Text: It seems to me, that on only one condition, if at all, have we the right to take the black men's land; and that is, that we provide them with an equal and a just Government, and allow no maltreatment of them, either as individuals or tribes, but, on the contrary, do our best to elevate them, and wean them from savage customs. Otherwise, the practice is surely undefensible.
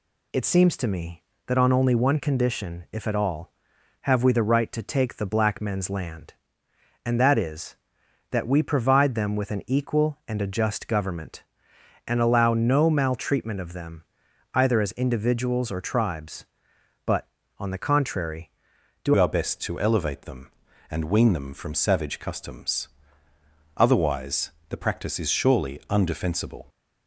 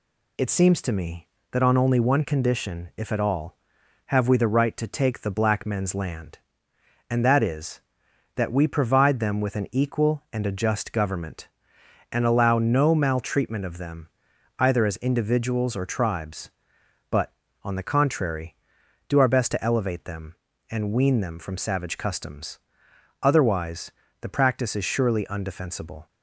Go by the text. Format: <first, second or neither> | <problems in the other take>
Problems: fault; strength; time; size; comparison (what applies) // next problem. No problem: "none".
second | changes voice at "our"; from 19.1 s on; 7.5 s long